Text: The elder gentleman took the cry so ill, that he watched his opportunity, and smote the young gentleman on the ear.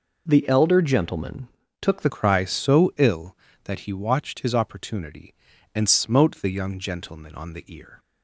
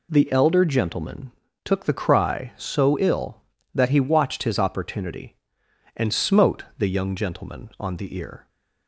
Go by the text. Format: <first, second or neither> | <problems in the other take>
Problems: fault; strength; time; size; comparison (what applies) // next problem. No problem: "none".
second | pauses between "gentleman" and "took"; slight; at 1.4 s; 0.34 s long; slight in the second // changes voice at "cry"; from 2.0 s on; 5.9 s long